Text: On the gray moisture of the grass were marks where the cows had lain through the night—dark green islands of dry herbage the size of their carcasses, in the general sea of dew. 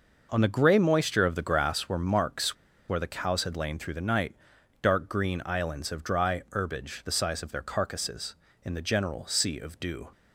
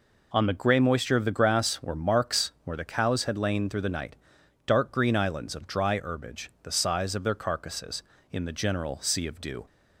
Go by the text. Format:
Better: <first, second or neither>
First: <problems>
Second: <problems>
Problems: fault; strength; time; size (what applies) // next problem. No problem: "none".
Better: second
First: pauses between "marks" and "where"; slight; at 2.5 s; 0.32 s long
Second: none